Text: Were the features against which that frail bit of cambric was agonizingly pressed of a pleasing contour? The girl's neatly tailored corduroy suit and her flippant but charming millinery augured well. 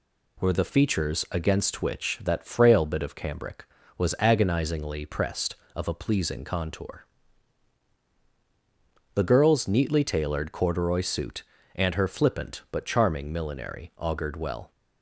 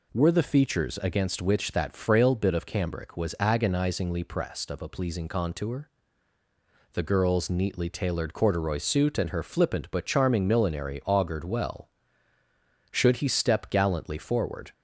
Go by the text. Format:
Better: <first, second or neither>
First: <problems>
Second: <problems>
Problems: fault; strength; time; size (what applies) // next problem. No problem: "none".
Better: first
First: none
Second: goes on to say "Should he step gallantly forward"; strong; from 12.9 s on; 1.8 s long